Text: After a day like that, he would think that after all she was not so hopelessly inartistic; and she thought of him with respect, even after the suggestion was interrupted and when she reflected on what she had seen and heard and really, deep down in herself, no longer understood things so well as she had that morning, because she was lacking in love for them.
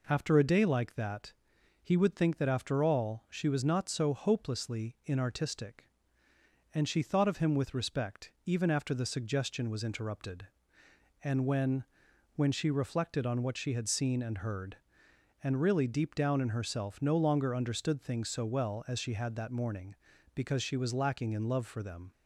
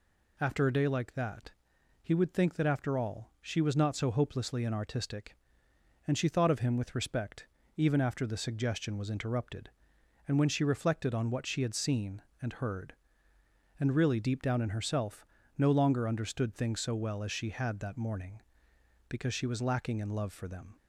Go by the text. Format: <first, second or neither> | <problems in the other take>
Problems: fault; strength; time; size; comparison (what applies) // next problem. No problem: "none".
second | says "when" twice; at 12.3 s